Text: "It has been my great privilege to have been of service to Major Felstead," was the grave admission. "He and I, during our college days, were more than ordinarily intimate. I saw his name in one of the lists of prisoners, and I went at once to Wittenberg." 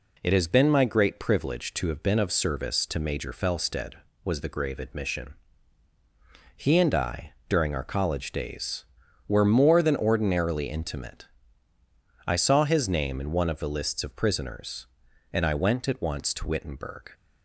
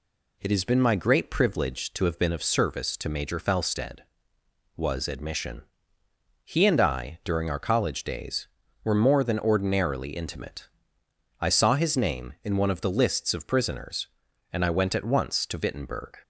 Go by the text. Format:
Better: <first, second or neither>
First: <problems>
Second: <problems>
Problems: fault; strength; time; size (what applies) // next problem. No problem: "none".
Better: first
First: none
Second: skips "the grave"; at 5.0 s